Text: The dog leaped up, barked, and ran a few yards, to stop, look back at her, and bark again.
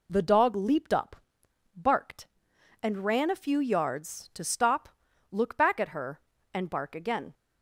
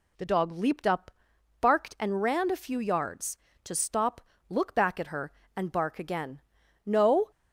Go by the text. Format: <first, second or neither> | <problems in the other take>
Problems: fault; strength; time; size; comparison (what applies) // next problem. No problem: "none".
first | goes on to say "No"; slight; from 6.8 s on; 0.44 s long